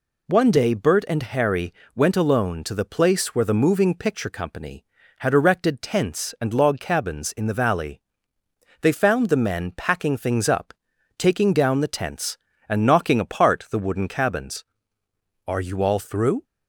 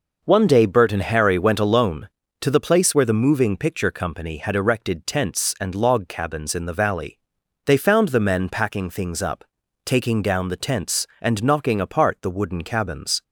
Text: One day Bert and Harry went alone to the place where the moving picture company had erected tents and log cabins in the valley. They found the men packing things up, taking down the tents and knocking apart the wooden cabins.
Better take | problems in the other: second | pauses between "Harry" and "went"; slight; at 1.7 s; 0.22 s long // goes on to say "Are you all through"; noticeable; from 15.4 s on; 0.98 s long

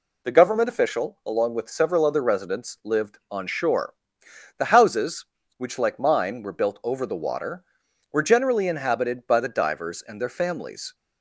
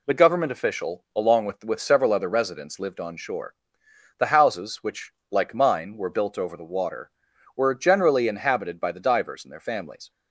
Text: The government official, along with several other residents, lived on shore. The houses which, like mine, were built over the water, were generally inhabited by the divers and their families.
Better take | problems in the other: first | says "with" twice; at 1.6 s

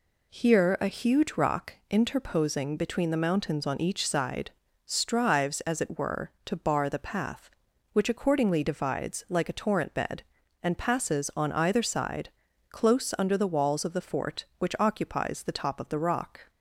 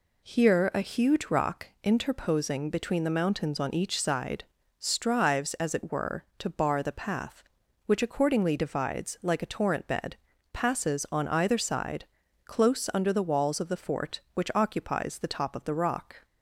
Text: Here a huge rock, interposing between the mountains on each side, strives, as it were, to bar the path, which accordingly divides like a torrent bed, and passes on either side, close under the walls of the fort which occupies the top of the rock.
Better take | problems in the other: first | skips "and"; at 10.3 s

